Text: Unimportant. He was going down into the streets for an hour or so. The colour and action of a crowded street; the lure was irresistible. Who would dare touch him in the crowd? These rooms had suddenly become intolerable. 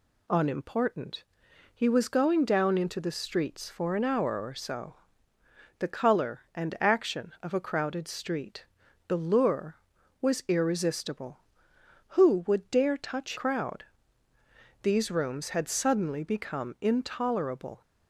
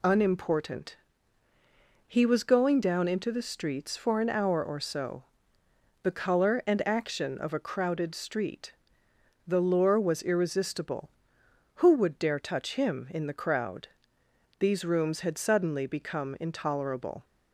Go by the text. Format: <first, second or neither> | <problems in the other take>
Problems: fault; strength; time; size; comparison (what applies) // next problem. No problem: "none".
second | skips "him in the"; at 13.3 s